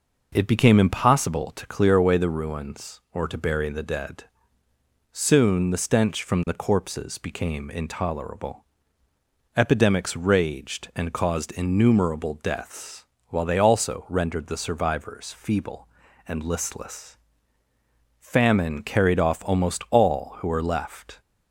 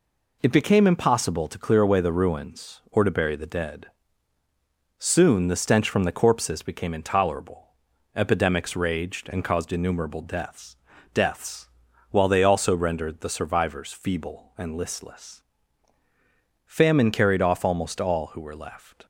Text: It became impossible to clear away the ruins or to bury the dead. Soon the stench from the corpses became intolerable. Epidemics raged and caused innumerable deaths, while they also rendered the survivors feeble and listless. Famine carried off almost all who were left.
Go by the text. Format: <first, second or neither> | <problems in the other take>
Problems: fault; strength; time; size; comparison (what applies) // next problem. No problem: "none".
first | says "deaths" twice; at 11.1 s